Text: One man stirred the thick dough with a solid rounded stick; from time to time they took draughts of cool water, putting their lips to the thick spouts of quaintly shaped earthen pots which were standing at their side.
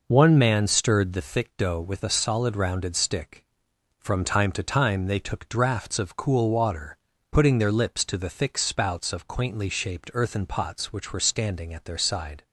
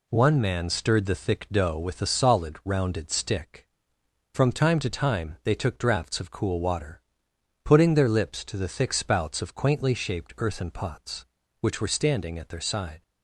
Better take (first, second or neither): neither